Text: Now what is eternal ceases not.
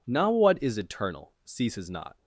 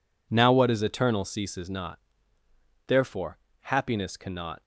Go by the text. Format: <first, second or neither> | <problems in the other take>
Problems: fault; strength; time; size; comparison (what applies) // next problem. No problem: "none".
first | goes on to say "Therefore Happiness cannot"; strong; from 2.8 s on; 1.7 s long